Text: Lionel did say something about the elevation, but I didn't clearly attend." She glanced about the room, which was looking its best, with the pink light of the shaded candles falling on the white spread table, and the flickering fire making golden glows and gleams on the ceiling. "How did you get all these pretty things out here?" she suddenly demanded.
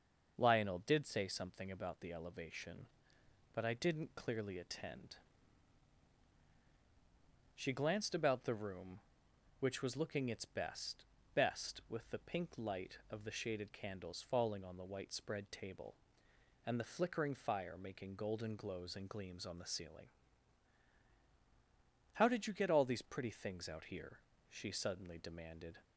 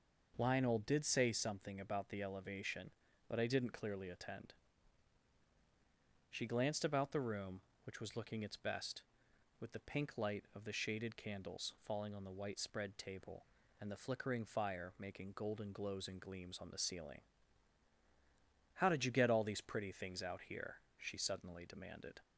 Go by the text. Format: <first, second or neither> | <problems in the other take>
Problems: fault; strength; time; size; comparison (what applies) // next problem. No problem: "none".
second | starts louder than the rest; until 1.3 s; 6 dB // says "best" twice; at 11.3 s